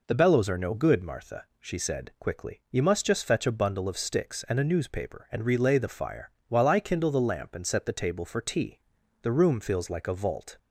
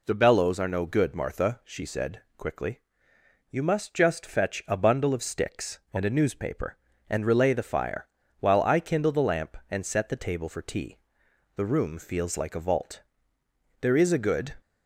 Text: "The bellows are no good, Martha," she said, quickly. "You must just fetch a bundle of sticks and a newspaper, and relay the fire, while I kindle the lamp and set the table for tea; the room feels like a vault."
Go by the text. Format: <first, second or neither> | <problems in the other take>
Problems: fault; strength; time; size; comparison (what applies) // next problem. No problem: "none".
first | goes on to say "There is a good"; noticeable; from 13.7 s on; 0.76 s long